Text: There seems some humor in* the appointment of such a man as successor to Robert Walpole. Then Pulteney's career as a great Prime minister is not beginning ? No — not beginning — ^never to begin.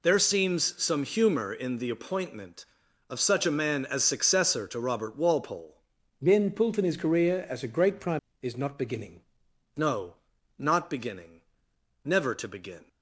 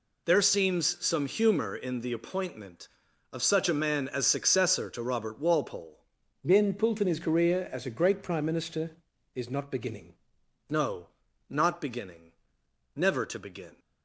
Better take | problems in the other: second | skips "minister"; at 8.3 s

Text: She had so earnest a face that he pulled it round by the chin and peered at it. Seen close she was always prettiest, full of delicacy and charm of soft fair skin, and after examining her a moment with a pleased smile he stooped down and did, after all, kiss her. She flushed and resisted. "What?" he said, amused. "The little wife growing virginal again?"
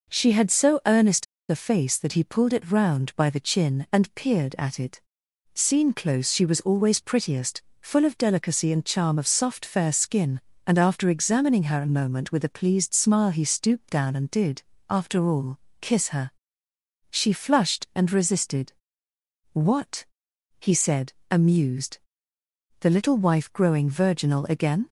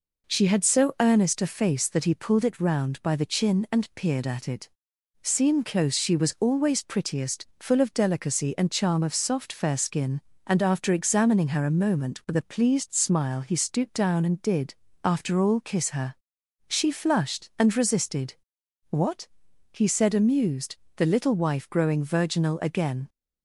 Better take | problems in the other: second | pauses between "earnest" and "a"; slight; at 1.2 s; 0.25 s long

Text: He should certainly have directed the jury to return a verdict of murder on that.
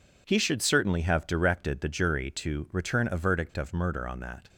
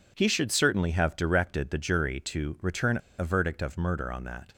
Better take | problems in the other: first | pauses between "return" and "a"; slight; at 2.9 s; 0.22 s long

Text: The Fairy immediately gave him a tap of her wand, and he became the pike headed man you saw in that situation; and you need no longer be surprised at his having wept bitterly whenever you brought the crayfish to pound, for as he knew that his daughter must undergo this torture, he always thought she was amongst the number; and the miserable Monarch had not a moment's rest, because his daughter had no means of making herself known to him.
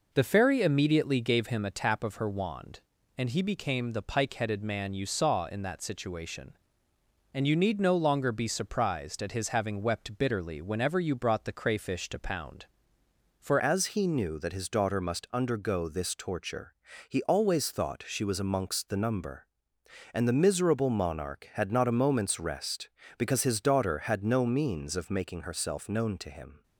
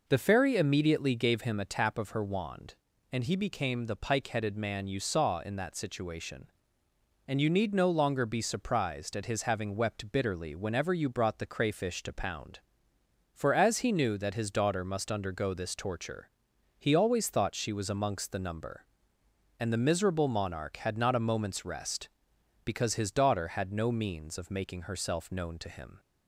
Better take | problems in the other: second | changes voice at "as"; from 13.5 s on; 13.1 s long

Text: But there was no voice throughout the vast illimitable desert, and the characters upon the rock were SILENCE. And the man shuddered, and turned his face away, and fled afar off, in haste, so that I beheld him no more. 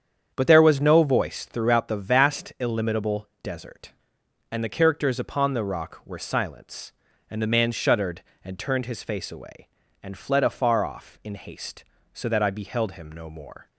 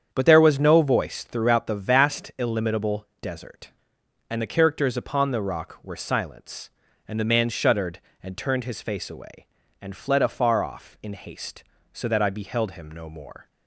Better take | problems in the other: neither | starts louder than the rest; strong; the same in both

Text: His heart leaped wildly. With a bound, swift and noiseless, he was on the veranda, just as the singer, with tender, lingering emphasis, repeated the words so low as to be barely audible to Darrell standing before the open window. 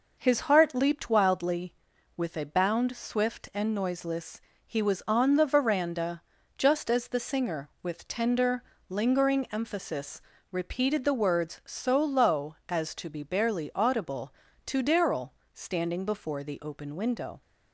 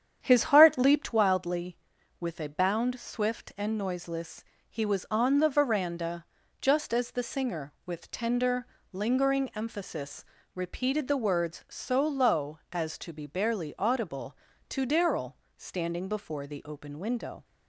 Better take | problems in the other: first | starts louder than the rest; strong; until 1.2 s; 8.5 dB // pauses between "Darrell" and "standing"; slight; at 15.3 s; 0.22 s long; slight in the first

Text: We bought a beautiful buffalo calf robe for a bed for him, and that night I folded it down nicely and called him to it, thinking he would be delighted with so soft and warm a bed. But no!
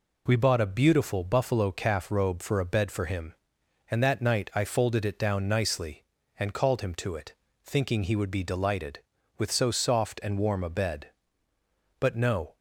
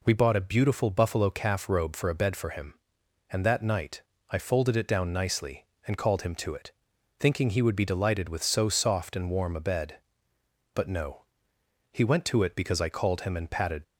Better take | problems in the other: first | pauses between "night" and "I"; slight; at 4.0 s; 0.30 s long // goes on to say "He went to it because I called him and patted"; strong; from 11.9 s on; 1.9 s long

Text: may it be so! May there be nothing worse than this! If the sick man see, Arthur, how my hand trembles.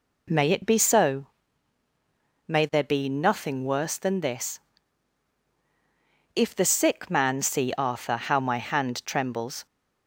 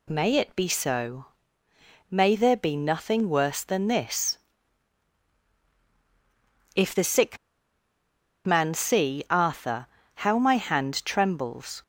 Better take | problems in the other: first | pauses between "sick" and "man"; at 7.3 s; 1.0 s long

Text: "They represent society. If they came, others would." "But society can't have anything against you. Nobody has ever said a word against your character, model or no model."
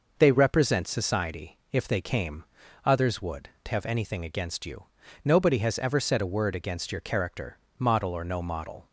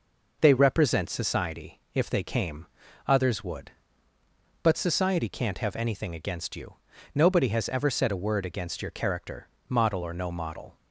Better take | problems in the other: second | skips "But society can't"; at 3.5 s

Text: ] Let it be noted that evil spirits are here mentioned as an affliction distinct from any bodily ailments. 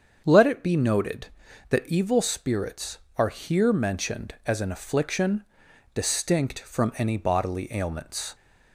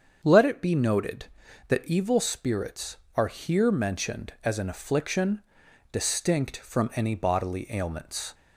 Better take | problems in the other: neither | starts louder than the rest; the same in both // pauses between "affliction" and "distinct"; noticeable; the same in both

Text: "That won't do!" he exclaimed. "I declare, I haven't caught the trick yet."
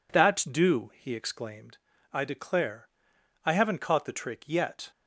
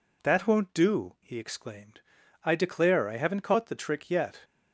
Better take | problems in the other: second | skips "won't"; at 0.4 s

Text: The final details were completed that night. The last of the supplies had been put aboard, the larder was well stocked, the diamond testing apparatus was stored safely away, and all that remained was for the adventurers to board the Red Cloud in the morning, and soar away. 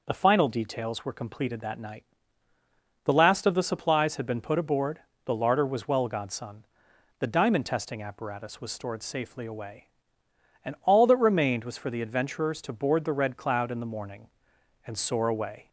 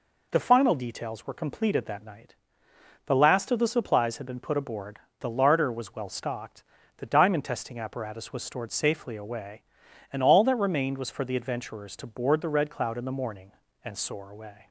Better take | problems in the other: second | says "godson" for "stocked"; at 6.0 s

